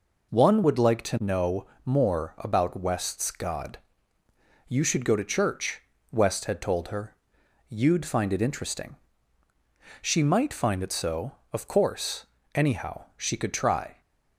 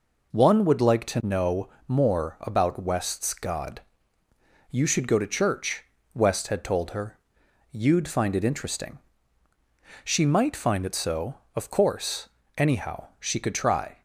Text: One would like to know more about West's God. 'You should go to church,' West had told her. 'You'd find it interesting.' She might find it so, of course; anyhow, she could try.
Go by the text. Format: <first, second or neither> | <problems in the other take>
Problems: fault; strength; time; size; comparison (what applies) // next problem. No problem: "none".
neither | pauses between "know" and "more"; slight; the same in both